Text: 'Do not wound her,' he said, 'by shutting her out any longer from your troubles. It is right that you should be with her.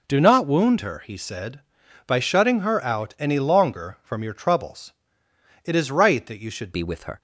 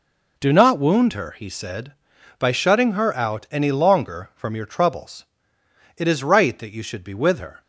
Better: second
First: changes voice at "be"; from 6.7 s on; 0.5 s long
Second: none

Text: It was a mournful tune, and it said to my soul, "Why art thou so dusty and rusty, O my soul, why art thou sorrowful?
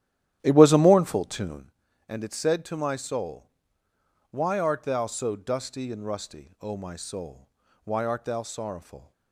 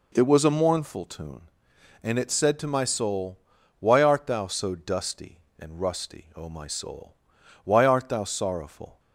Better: second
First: starts louder than the rest; strong; until 1.7 s; 12 dB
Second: none

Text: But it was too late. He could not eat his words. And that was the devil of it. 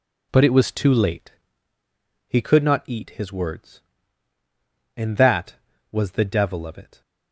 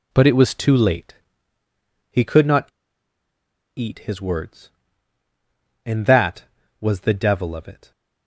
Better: first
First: none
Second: pauses between "not" and "eat"; at 2.6 s; 1.1 s long

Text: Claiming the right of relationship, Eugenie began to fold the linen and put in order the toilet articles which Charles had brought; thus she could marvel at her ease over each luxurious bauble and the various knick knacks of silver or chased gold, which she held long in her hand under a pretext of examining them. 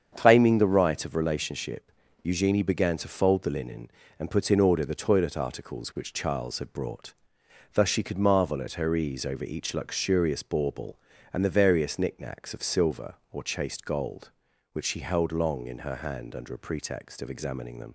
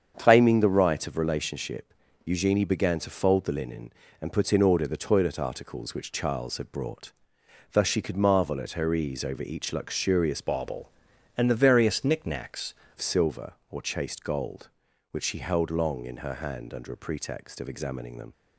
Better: first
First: starts louder than the rest; strong; until 1.1 s; 7.5 dB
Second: starts louder than the rest; strong; until 1.1 s; 7.5 dB // changes voice from "bauble" to "knacks"; from 10.4 to 12.7 s; 2.3 s long

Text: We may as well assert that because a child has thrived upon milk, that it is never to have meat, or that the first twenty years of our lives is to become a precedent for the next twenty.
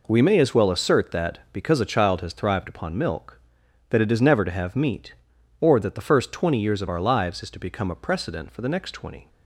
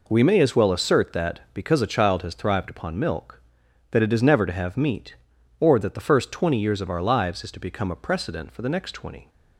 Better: neither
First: none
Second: none

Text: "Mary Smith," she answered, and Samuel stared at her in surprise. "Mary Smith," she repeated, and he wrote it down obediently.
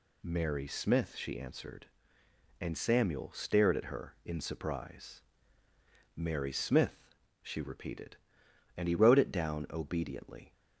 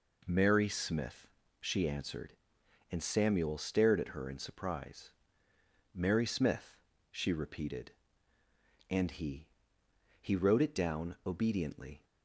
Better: first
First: none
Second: says "he" twice; at 10.2 s

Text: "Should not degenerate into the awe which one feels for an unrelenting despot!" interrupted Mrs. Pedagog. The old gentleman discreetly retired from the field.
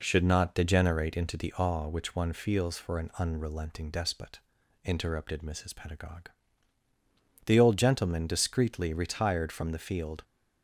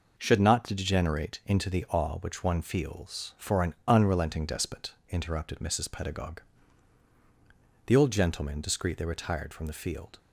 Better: neither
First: none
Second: none

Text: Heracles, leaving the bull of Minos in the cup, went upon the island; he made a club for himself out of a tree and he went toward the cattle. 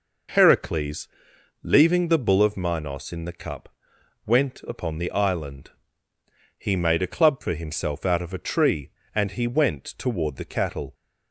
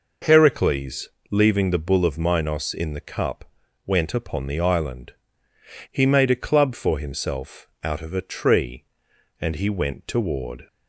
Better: first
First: none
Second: pauses between "himself" and "out"; slight; at 7.6 s; 0.16 s long // stops before "the cattle"; at 10.6 s

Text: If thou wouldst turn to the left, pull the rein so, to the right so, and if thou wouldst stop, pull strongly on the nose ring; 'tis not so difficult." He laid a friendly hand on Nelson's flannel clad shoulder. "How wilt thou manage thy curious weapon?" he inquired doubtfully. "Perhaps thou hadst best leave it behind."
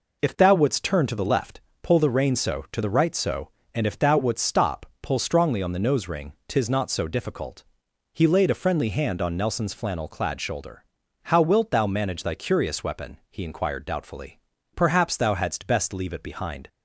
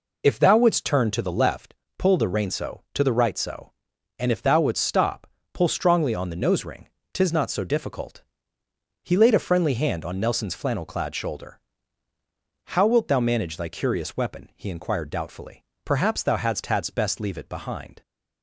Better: first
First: none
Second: says "hadst" twice; at 16.6 s

